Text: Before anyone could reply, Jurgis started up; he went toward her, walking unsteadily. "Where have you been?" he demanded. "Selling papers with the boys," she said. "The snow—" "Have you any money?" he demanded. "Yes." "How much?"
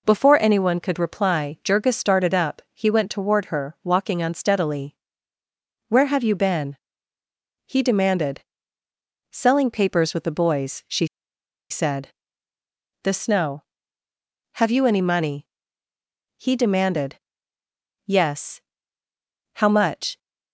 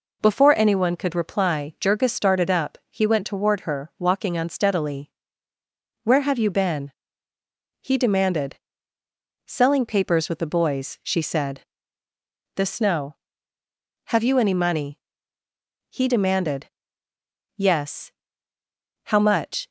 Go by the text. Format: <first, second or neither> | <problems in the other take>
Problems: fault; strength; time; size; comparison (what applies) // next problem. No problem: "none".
second | pauses between "she" and "said"; noticeable; at 11.0 s; 0.64 s long